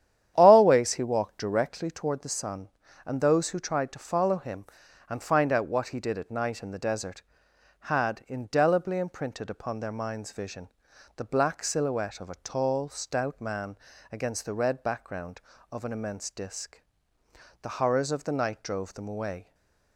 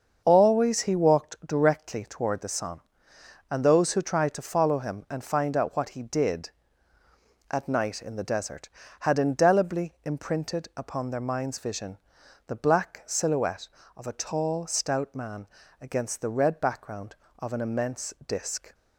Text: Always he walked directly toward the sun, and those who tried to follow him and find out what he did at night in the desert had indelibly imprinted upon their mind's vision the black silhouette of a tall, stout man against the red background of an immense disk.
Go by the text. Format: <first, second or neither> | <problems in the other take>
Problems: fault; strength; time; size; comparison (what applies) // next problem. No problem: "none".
second | starts louder than the rest; strong; until 1.3 s; 10 dB; also in the second // pauses between "vision" and "the"; noticeable; at 10.6 s; 0.46 s long; noticeable in the second // pauses between "man" and "against"; slight; at 13.7 s; 0.34 s long; slight in the second // goes on to say "The horrors of the night drove them away"; strong; from 17.6 s on; 1.9 s long // stays silent after the last word; slight; from 19.4 s on; 0.5 s long